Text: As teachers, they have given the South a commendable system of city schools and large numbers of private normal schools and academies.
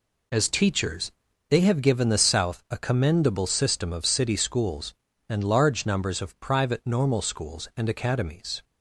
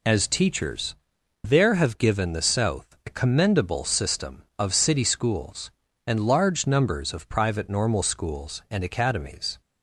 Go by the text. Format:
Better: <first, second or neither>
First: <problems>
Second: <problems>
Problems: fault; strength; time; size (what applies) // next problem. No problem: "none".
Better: first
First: none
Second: says "there" for "they"; at 1.4 s